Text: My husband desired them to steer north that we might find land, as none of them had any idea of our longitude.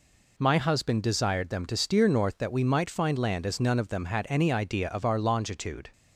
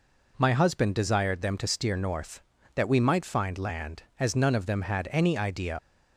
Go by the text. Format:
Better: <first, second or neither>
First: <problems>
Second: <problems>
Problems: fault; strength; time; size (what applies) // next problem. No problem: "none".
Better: first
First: none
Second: stops before "of our longitude"; at 5.7 s